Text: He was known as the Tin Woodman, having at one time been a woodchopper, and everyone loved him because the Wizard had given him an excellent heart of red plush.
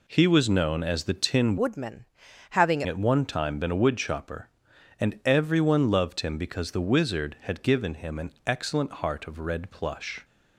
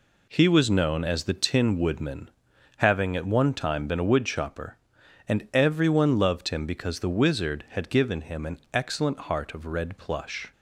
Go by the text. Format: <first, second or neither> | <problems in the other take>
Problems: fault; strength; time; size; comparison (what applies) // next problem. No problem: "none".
second | changes voice from "Woodman" to "having"; from 1.5 to 2.8 s; 1.3 s long // pauses between "an" and "excellent"; slight; at 8.3 s; 0.16 s long; slight in the second